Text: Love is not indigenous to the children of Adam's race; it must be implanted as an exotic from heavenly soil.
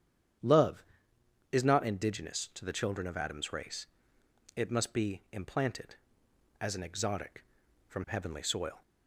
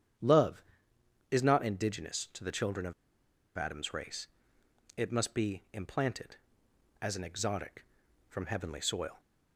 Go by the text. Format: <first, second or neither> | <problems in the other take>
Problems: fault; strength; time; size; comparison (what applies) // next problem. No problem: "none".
first | starts louder than the rest; strong; until 1.8 s; 9 dB; strong in the first // pauses between "of" and "Adam's"; noticeable; at 2.9 s; 0.64 s long